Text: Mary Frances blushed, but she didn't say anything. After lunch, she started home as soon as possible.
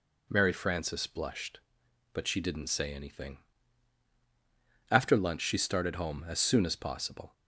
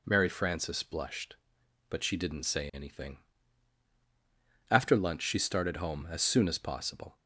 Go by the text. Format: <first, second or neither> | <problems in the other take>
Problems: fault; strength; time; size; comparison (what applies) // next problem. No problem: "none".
neither | none